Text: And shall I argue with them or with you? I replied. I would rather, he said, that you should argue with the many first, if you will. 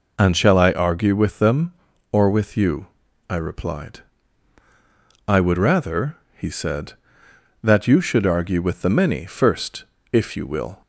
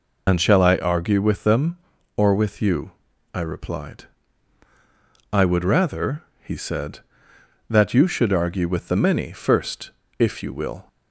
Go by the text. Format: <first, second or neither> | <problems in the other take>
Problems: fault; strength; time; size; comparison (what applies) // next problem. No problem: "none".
first | loses the start of "And"; at 0.2 s; 45 ms